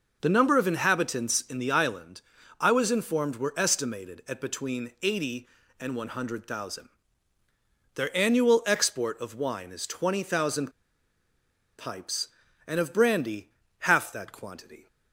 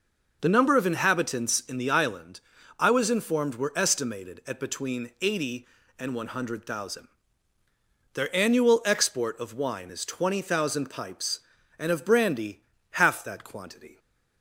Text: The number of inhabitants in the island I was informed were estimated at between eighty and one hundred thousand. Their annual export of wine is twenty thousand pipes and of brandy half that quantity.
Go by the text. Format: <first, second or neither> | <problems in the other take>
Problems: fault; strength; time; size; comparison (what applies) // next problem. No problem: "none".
second | pauses between "island" and "I"; at 2.1 s; 0.40 s long; also in the second // pauses between "thousand" and "pipes"; at 10.6 s; 1.0 s long // pauses between "brandy" and "half"; slight; at 13.4 s; 0.30 s long; slight in the second